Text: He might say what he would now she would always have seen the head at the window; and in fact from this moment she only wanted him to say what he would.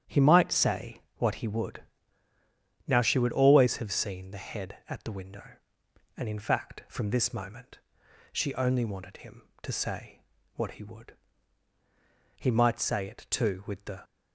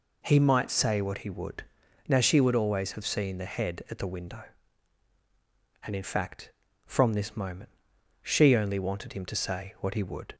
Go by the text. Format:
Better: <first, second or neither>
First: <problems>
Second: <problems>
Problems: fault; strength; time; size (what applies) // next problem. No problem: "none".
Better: second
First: starts louder than the rest; strong; until 1.2 s; 9.5 dB // pauses between "say" and "what"; slight; at 1.0 s; 0.16 s long // pauses between "would" and "now"; at 1.8 s; 1.0 s long // pauses between "moment" and "she"; noticeable; at 7.7 s; 0.52 s long // pauses between "say" and "what"; slight; at 10.1 s; 0.34 s long // goes on to say "He might say it too with the"; from 12.3 s on; 1.6 s long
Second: pauses between "would" and "now"; at 1.6 s; 0.42 s long // pauses between "moment" and "she"; noticeable; at 7.7 s; 0.52 s long